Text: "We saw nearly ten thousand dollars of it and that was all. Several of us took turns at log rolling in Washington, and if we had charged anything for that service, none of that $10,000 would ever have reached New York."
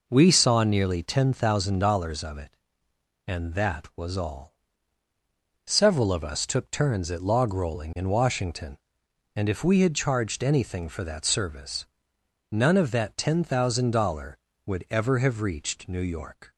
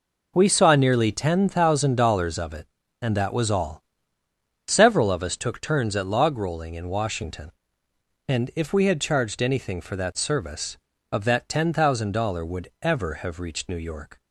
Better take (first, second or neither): first